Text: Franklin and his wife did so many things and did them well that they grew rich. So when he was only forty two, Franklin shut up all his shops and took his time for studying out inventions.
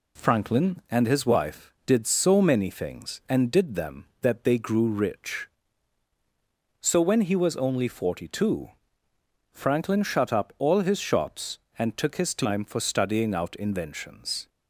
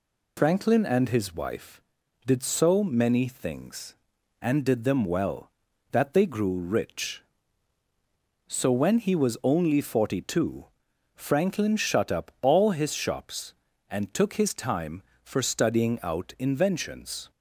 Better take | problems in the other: second | skips "well"; at 4.1 s

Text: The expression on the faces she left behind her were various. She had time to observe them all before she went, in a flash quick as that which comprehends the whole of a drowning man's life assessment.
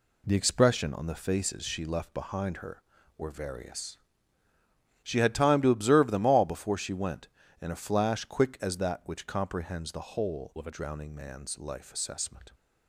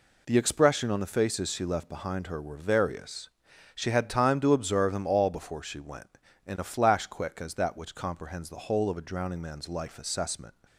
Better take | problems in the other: second | changes voice from "of" to "a"; from 10.5 to 10.7 s; 0.2 s long

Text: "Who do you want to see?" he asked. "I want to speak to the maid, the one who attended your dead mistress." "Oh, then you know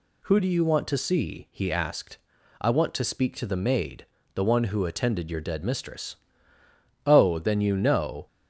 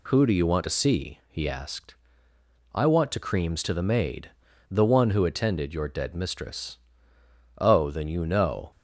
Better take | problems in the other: first | says "creams" for "speak"; at 3.1 s

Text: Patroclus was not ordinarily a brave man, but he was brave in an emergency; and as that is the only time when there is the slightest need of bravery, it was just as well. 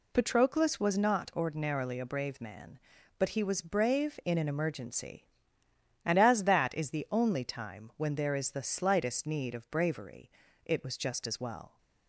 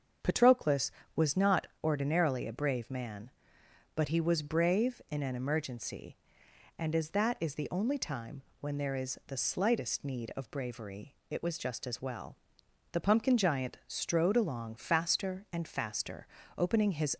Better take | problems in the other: first | starts louder than the rest; until 1.4 s; 7 dB // pauses between "not" and "ordinarily"; slight; at 1.6 s; 0.16 s long // pauses between "time" and "when"; slight; at 8.4 s; 0.18 s long // goes on to say "The Pumpkin Giant strode along faster and faster opening his"; strong; from 12.9 s on; 4.2 s long

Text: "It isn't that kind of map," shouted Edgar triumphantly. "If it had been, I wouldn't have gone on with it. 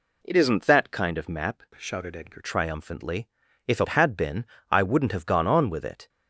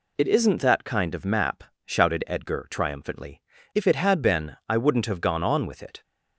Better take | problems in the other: second | changes voice from "shouted" to "Edgar"; from 1.7 to 2.3 s; 0.6 s long

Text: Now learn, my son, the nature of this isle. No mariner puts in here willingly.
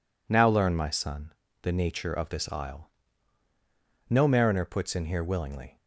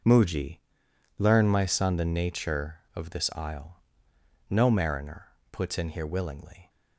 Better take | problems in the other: first | says "Muji" for "Now"; at 0.0 s // pauses between "mariner" and "puts"; slight; at 5.2 s; 0.24 s long

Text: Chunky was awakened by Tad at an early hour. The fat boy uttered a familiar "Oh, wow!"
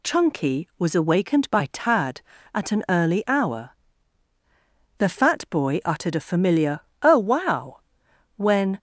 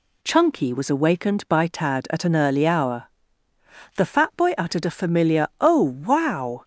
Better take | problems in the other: second | pauses between "familiar" and "Oh"; slight; at 6.7 s; 0.22 s long // goes on to say "when"; slight; from 8.3 s on; 0.42 s long

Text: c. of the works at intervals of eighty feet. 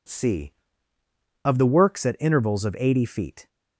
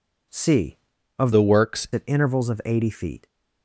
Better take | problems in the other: first | changes voice from "the" to "works"; from 1.3 to 1.8 s; 0.5 s long

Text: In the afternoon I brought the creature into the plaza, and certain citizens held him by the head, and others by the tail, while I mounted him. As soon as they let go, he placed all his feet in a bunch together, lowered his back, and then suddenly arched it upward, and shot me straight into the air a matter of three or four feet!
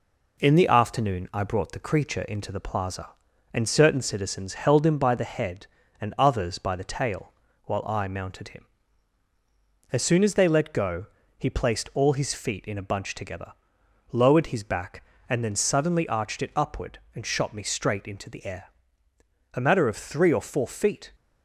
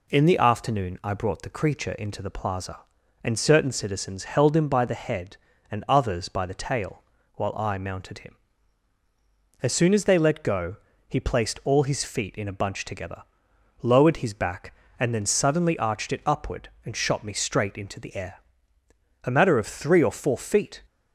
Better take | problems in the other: second | gets quieter; slight; throughout; 2.5 dB // pauses between "air" and "a"; noticeable; at 18.6 s; 0.86 s long; noticeable in the second

